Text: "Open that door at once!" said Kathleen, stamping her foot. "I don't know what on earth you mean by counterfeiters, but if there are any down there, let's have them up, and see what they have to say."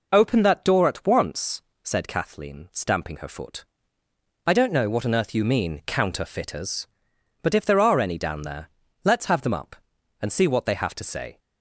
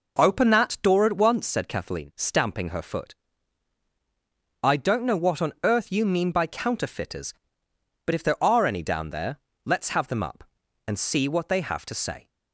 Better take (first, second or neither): second